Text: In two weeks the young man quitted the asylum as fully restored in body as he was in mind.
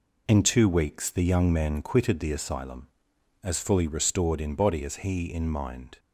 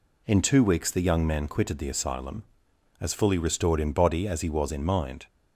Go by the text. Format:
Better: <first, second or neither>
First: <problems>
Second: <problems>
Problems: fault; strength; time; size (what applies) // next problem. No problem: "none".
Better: second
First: skips "was"; at 5.3 s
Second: none